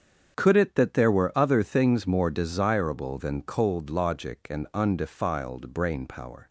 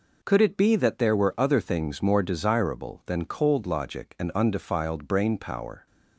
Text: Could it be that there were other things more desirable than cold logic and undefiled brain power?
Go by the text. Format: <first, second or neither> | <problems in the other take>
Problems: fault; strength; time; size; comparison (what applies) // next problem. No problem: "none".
second | starts louder than the rest; strong; until 1.4 s; 8 dB // skips "be"; at 0.7 s